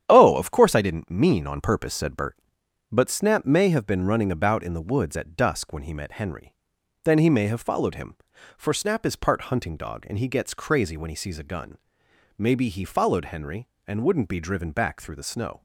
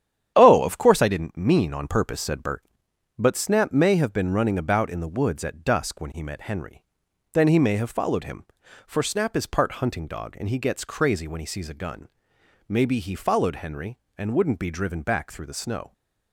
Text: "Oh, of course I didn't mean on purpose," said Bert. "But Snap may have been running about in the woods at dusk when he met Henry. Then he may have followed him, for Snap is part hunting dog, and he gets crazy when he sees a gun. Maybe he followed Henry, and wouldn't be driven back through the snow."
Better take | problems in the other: neither | starts louder than the rest; strong; the same in both

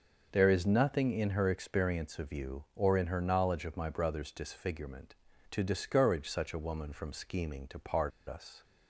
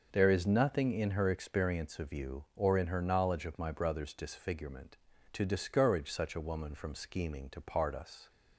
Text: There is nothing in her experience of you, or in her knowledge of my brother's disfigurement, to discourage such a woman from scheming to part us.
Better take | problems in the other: second | pauses between "part" and "us"; slight; at 8.1 s; 0.17 s long

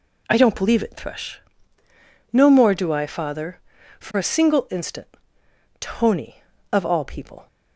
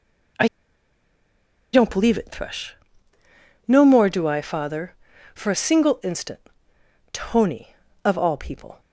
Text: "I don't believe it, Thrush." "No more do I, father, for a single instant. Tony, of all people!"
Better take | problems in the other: first | pauses between "I" and "don't"; strong; at 0.4 s; 1.2 s long

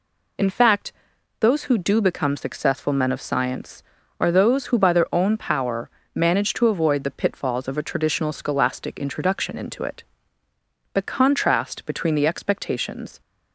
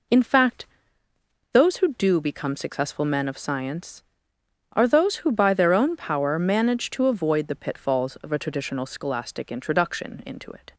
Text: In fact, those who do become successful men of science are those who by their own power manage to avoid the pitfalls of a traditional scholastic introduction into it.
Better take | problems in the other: second | pauses between "power" and "manage"; slight; at 5.9 s; 0.24 s long // goes on to say "The contrast between the expectations"; strong; from 10.9 s on; 2.2 s long

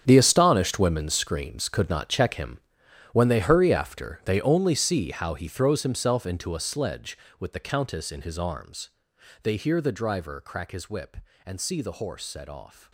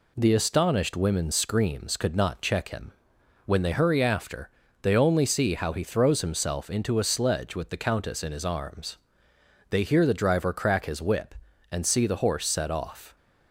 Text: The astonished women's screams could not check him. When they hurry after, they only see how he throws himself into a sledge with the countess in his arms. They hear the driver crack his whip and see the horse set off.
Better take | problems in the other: second | gets quieter; strong; throughout; 14 dB

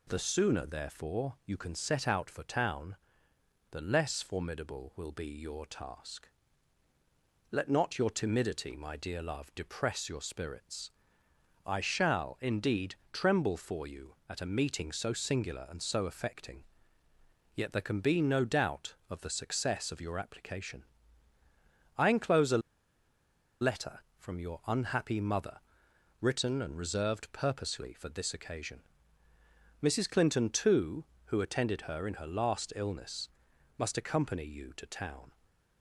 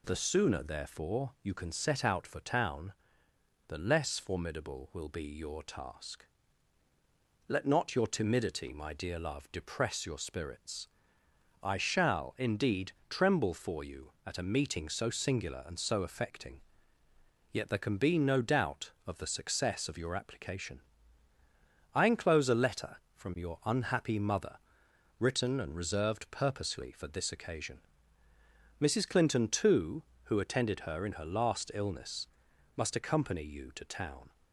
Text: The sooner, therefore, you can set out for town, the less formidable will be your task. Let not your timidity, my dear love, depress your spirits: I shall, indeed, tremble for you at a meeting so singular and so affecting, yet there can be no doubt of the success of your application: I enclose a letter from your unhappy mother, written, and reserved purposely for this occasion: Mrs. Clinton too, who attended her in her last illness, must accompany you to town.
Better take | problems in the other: second | pauses between "a" and "letter"; at 22.6 s; 1.0 s long

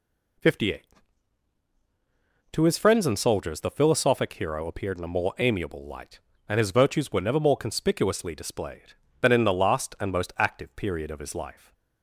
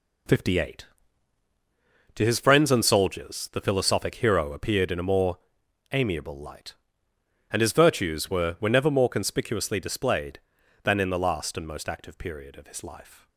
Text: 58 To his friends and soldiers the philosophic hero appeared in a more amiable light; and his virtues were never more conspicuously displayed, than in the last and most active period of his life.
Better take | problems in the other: first | pauses between "more" and "amiable"; noticeable; at 5.3 s; 0.56 s long // says "were" twice; at 8.5 s

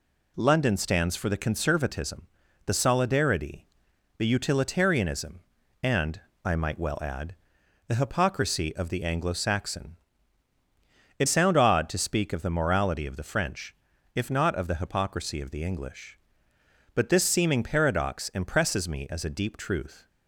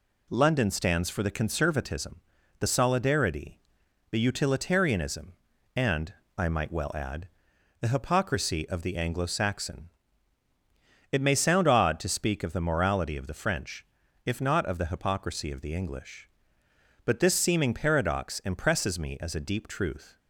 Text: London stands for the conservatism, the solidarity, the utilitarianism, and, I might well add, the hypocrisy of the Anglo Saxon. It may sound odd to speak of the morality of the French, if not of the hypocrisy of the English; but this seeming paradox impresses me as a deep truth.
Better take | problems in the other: second | skips "may"; at 11.2 s

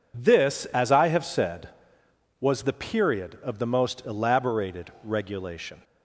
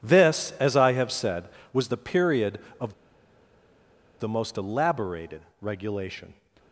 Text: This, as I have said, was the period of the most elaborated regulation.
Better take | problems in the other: first | pauses between "of" and "the"; strong; at 2.9 s; 1.2 s long // pauses between "elaborated" and "regulation"; slight; at 5.4 s; 0.18 s long

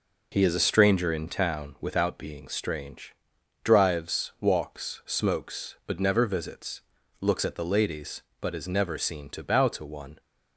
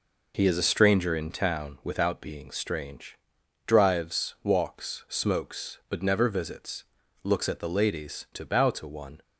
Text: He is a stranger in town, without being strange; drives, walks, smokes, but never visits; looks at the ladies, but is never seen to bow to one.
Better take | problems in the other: first | skips "but is never seen"; at 8.2 s

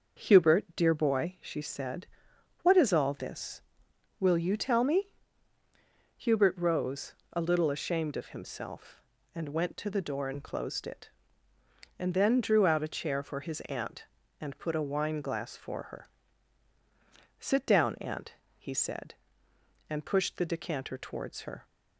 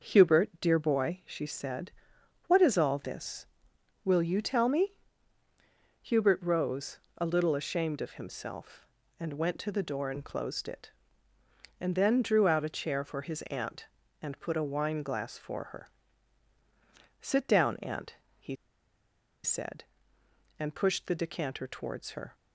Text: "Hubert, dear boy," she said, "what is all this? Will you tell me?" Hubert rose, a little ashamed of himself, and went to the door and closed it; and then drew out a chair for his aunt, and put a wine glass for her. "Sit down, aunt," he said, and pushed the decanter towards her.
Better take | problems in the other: first | starts louder than the rest; until 1.1 s; 6.5 dB; also in the first // pauses between "he" and "said"; noticeable; at 18.5 s; 0.88 s long

